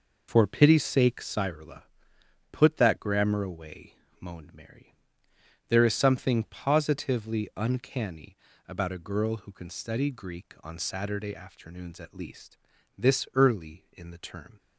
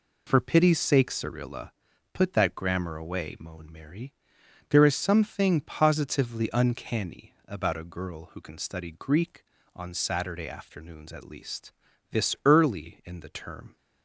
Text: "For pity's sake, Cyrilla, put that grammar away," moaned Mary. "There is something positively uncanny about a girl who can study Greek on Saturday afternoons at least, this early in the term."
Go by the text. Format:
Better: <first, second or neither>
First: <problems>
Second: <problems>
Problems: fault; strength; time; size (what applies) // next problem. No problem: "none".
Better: second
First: loses the start of "For"; at 0.2 s; 30 ms // pauses between "uncanny" and "about"; slight; at 8.3 s; 0.30 s long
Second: none